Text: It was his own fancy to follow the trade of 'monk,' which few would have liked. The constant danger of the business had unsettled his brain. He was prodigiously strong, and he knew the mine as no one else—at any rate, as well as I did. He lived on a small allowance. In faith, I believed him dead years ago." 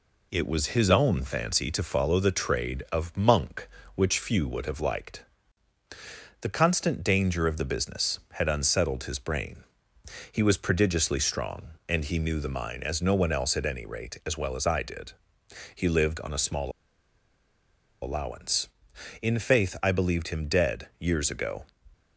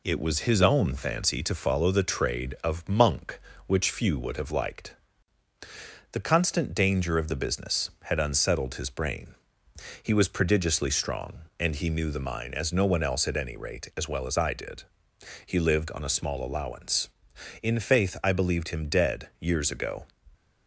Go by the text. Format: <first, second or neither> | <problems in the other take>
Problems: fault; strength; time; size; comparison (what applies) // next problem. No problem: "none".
second | pauses between "small" and "allowance"; strong; at 16.7 s; 1.3 s long